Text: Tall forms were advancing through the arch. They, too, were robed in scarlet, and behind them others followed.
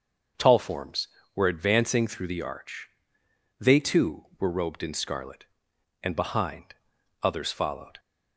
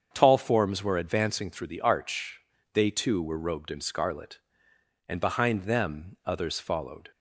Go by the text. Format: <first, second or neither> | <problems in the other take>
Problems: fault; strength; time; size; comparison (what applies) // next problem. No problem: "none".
second | starts louder than the rest; until 1.6 s; 6.5 dB; strong in the second // skips "them"; at 6.9 s